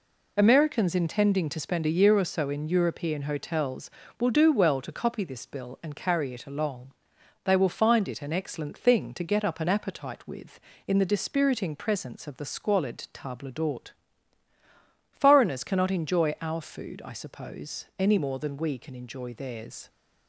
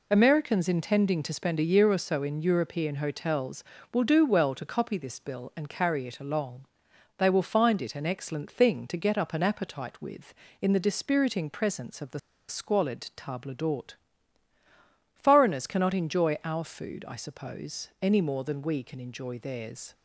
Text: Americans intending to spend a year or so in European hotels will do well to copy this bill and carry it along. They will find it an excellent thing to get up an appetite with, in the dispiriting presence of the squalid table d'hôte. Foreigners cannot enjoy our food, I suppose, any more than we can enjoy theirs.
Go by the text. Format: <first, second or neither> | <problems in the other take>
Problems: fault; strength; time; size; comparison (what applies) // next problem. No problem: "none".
first | pauses between "the" and "squalid"; slight; at 12.1 s; 0.29 s long